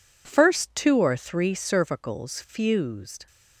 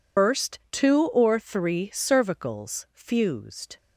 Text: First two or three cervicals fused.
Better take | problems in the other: first | loses the start of "First"; at 0.1 s; 125 ms

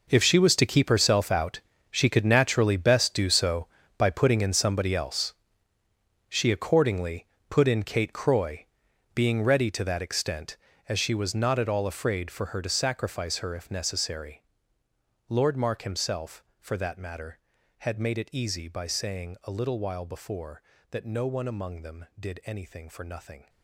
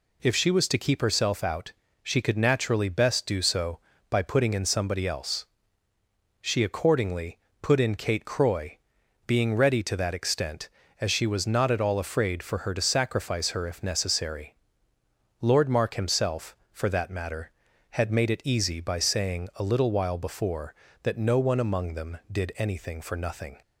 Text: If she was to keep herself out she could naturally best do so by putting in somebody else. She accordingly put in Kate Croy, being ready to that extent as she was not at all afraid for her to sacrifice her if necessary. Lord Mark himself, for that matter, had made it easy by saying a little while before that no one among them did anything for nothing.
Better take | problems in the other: second | gets quieter; strong; throughout; 15.5 dB // pauses between "out" and "she"; slight; at 1.5 s; 0.30 s long; slight in the second // pauses between "accordingly" and "put"; slight; at 7.2 s; 0.24 s long; slight in the second

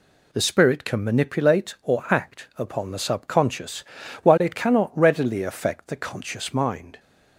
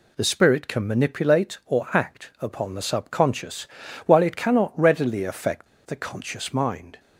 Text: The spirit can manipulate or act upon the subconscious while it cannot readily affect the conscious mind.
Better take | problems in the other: first | pauses between "subconscious" and "while"; at 3.6 s; 0.38 s long; also in the first // pauses between "affect" and "the"; slight; at 5.6 s; 0.20 s long

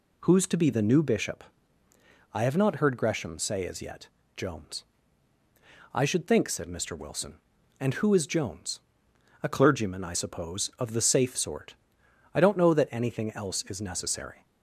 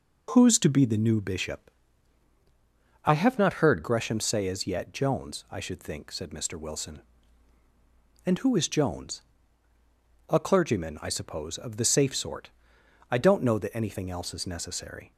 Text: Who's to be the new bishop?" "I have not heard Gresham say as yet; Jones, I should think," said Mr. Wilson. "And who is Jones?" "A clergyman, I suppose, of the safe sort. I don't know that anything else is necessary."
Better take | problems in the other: first | changes voice from "not" to "heard"; from 3.3 to 3.8 s; 0.5 s long

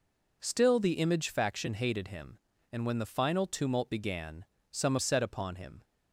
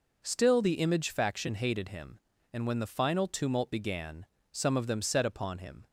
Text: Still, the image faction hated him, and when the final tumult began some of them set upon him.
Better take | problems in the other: second | pauses between "began" and "some"; slight; at 4.4 s; 0.26 s long; slight in the second // skips "of them"; at 4.9 s

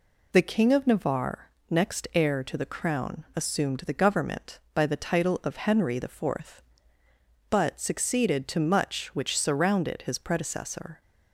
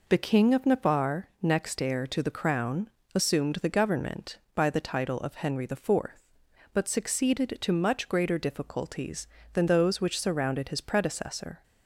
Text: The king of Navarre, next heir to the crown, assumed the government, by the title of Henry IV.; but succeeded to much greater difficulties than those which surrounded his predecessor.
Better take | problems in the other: second | skips "greater difficulties than those"; at 9.1 s

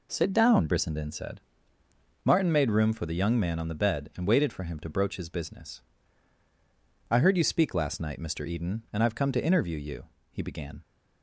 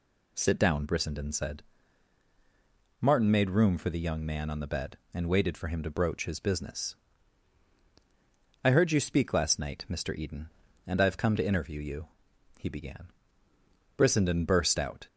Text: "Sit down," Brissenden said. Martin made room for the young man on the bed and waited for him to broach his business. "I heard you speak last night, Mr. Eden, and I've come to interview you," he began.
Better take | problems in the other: first | goes on to say "Brissenden burst out"; noticeable; from 13.9 s on; 1.1 s long

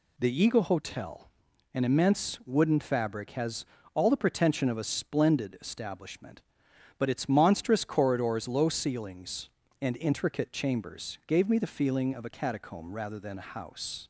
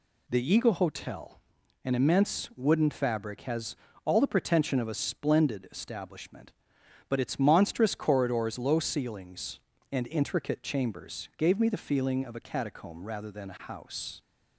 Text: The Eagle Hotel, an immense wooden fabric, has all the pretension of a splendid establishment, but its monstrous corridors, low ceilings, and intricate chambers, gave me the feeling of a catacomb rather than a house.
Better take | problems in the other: neither | pauses between "has" and "all"; slight; the same in both

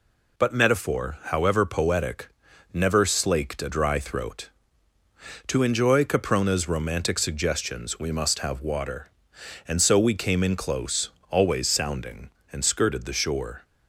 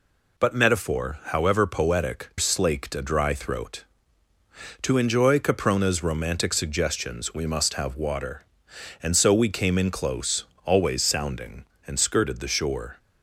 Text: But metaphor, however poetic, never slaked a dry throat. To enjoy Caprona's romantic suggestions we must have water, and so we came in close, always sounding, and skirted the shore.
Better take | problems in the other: first | skips "never"; at 2.3 s

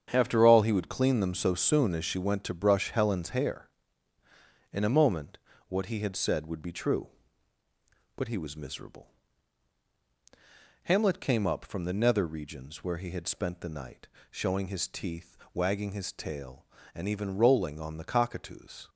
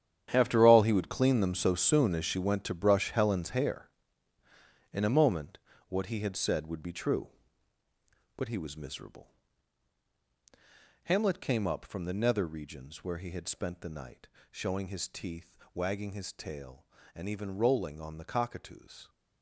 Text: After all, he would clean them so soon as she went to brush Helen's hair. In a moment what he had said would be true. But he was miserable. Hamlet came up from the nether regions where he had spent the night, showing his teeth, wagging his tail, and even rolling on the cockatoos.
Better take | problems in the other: first | gets quieter; strong; throughout; 14 dB // starts louder than the rest; strong; until 1.3 s; 9.5 dB; strong in the first // pauses between "moment" and "what"; slight; at 5.5 s; 0.32 s long; slight in the first

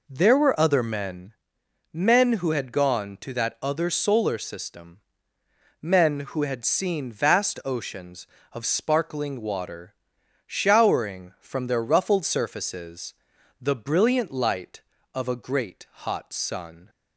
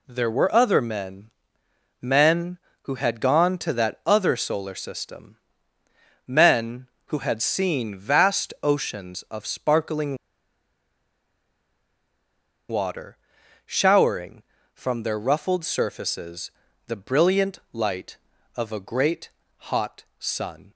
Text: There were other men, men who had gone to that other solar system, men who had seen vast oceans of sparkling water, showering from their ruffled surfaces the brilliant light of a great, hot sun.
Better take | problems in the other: first | pauses between "sparkling" and "water"; strong; at 10.1 s; 2.5 s long // pauses between "surfaces" and "the"; at 16.4 s; 0.38 s long; noticeable in the first

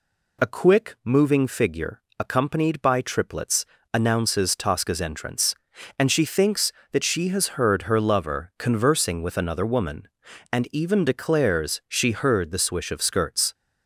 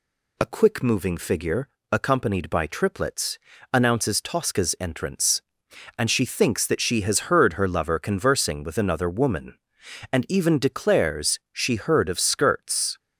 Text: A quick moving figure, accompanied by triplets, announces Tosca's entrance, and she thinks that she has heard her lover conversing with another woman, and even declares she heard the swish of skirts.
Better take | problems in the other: first | skips "the swish"; at 12.0 s

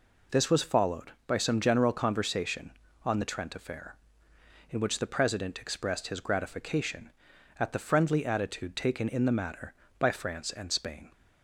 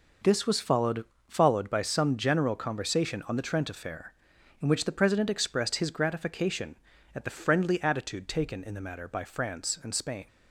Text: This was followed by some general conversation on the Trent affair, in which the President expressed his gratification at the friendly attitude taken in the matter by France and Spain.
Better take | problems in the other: first | says "followed" twice; at 1.2 s

